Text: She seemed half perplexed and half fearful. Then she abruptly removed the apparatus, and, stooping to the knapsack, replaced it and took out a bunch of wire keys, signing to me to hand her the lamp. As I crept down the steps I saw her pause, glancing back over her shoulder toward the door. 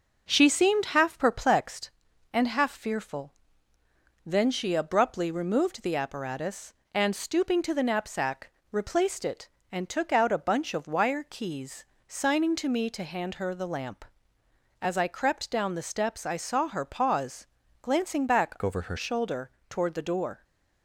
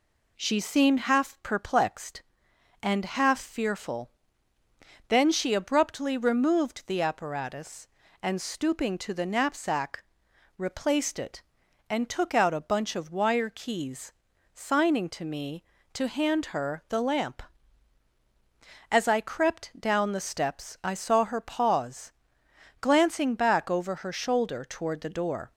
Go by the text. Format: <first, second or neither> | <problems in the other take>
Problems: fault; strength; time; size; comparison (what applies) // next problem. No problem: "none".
second | starts louder than the rest; noticeable; until 1.3 s; 6 dB // changes voice from "over" to "her"; from 18.6 to 18.9 s; 0.3 s long // pauses between "shoulder" and "toward"; slight; at 19.5 s; 0.18 s long